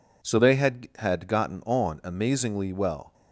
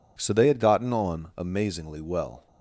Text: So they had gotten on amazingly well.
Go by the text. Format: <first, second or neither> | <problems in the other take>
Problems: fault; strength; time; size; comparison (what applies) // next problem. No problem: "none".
second | says "had" twice; at 0.9 s